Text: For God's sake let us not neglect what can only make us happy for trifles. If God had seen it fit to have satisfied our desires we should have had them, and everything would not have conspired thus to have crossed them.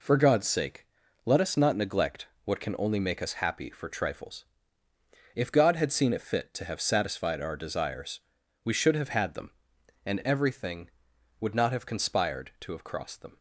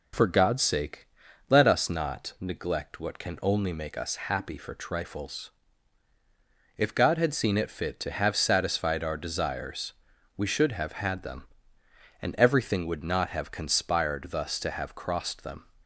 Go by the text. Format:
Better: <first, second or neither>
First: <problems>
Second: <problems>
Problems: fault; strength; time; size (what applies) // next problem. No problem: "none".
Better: second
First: pauses between "sake" and "let"; at 0.8 s; 0.38 s long // pauses between "neglect" and "what"; slight; at 2.2 s; 0.18 s long // pauses between "desires" and "we"; at 8.1 s; 0.44 s long // skips "thus"; at 12.5 s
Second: pauses between "sake" and "let"; at 1.0 s; 0.40 s long // pauses between "desires" and "we"; at 9.9 s; 0.44 s long